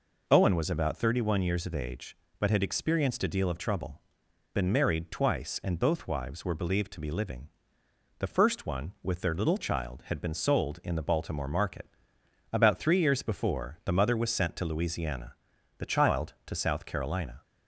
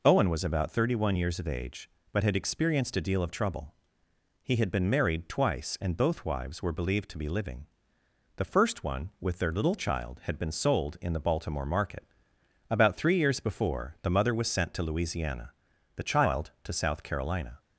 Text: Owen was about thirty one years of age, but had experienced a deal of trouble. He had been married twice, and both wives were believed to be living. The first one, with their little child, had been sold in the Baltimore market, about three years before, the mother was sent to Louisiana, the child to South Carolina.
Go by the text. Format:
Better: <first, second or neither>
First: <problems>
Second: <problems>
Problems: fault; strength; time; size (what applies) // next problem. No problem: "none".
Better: second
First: skips "He had"; at 4.2 s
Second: none